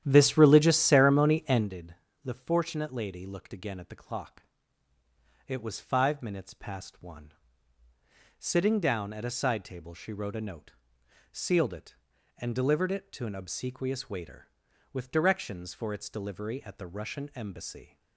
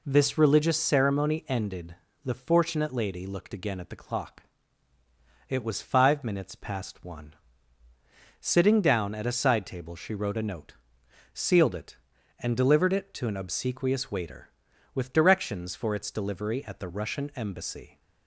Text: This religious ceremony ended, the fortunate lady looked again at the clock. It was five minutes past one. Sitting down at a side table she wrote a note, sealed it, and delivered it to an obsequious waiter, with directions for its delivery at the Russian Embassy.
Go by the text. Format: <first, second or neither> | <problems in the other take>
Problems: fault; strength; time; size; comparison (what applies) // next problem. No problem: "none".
second | starts louder than the rest; strong; until 1.7 s; 11 dB